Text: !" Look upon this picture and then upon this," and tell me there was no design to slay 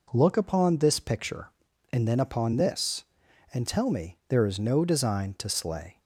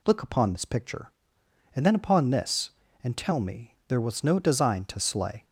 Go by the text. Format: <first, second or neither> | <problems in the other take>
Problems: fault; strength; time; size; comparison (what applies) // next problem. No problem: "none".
second | says "is" for "was"; at 4.4 s